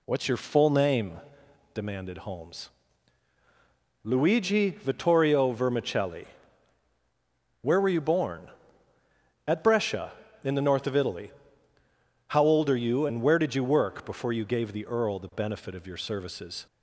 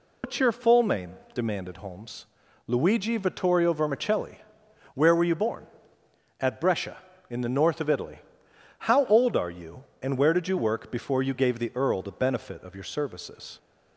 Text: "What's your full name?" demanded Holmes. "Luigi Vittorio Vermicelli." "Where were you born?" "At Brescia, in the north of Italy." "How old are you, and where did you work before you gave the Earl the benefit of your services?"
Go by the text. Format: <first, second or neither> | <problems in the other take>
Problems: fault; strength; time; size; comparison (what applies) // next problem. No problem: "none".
first | loses the start of "What's"; at 0.2 s; 135 ms